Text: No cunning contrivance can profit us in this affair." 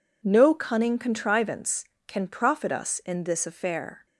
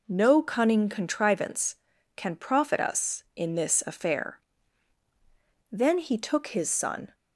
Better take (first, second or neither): first